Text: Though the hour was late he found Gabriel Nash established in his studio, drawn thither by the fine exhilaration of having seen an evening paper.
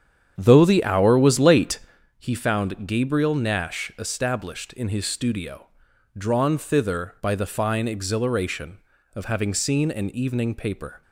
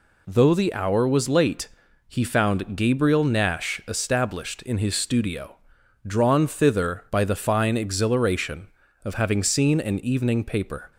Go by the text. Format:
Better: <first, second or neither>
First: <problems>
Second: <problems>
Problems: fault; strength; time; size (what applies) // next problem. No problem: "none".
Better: second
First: starts louder than the rest; strong; until 2.1 s; 8.5 dB // pauses between "late" and "he"; at 1.7 s; 0.38 s long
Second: pauses between "late" and "he"; at 1.6 s; 0.38 s long